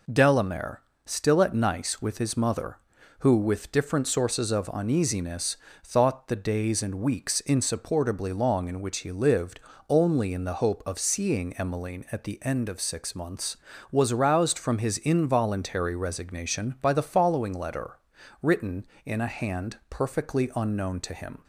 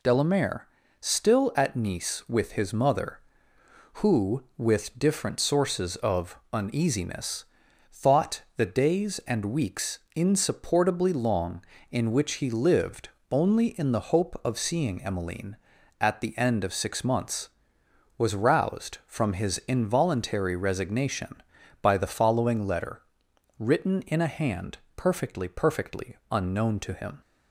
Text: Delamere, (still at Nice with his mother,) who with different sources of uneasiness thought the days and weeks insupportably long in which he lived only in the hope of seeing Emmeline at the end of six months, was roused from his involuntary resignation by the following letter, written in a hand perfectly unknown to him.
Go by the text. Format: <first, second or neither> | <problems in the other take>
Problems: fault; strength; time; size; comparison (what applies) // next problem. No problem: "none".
first | pauses between "of" and "uneasiness"; slight; at 6.3 s; 0.16 s long // pauses between "uneasiness" and "thought"; noticeable; at 7.4 s; 0.48 s long; slight in the first // pauses between "thought" and "the"; slight; at 8.4 s; 0.16 s long // pauses between "weeks" and "insupportably"; slight; at 9.9 s; 0.16 s long // pauses between "lived" and "only"; slight; at 13.1 s; 0.20 s long; slight in the first // pauses between "hand" and "perfectly"; slight; at 24.7 s; 0.18 s long // says "perfectly" twice; at 25.4 s